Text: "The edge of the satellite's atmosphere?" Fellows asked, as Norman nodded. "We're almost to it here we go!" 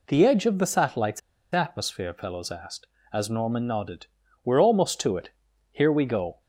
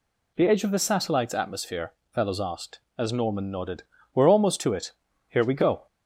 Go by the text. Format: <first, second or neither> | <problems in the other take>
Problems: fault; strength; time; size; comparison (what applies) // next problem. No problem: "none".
second | pauses between "satellite's" and "atmosphere"; slight; at 1.2 s; 0.34 s long // pauses between "it" and "here"; at 5.3 s; 0.40 s long; slight in the second